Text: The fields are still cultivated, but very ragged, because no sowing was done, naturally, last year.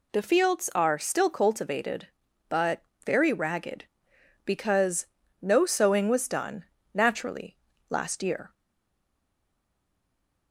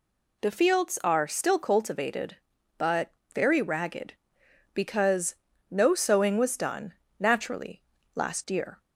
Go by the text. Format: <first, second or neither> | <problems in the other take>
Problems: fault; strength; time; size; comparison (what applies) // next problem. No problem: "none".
second | pauses between "but" and "very"; slight; at 2.8 s; 0.24 s long; slight in the second // pauses between "because" and "no"; slight; at 5.0 s; 0.34 s long; slight in the second // stays silent after the last word; noticeable; from 8.5 s on; 2.0 s long